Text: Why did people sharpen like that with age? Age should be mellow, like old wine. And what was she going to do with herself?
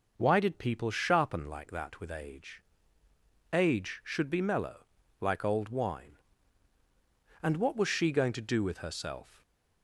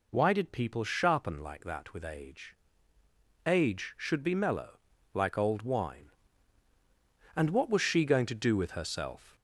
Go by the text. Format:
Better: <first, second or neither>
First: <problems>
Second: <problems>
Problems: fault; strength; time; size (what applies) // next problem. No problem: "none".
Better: first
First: none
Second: gets louder; slight; throughout; 3 dB